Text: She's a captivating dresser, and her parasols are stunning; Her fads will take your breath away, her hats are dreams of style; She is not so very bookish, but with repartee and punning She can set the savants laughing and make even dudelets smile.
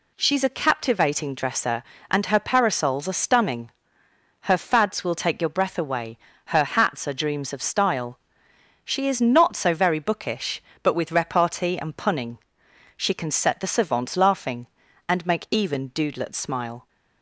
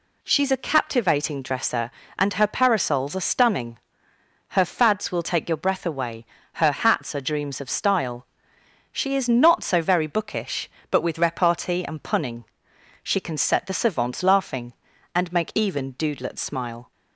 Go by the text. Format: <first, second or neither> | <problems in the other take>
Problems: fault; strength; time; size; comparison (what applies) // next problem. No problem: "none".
neither | pauses between "punning" and "She"; noticeable; the same in both